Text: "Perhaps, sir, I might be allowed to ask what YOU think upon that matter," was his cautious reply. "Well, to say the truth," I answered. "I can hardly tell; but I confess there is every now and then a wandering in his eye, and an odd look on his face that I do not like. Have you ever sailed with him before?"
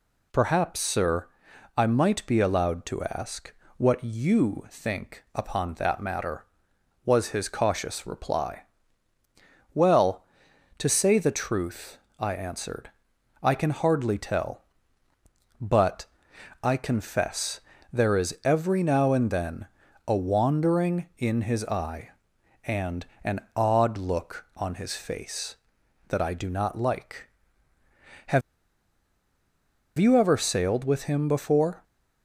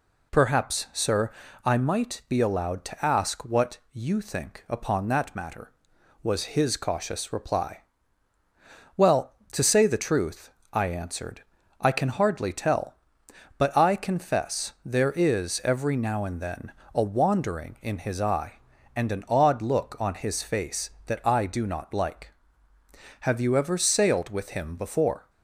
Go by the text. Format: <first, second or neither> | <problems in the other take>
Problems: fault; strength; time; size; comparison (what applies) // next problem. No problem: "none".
second | pauses between "ask" and "what"; slight; at 3.5 s; 0.26 s long // pauses between "but" and "I"; noticeable; at 16.0 s; 0.56 s long // pauses between "confess" and "there"; slight; at 17.5 s; 0.32 s long // pauses between "then" and "a"; at 19.6 s; 0.40 s long; slight in the second // pauses between "and" and "an"; slight; at 23.0 s; 0.20 s long // pauses between "Have" and "you"; strong; at 28.4 s; 1.5 s long